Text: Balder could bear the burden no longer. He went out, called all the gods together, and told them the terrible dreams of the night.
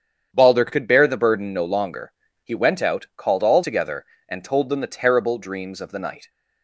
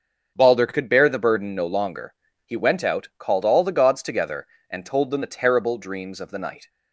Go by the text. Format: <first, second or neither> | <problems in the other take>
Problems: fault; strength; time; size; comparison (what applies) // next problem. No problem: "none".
second | starts louder than the rest; strong; until 1.3 s; 8.5 dB; also in the second // skips "the gods"; at 3.6 s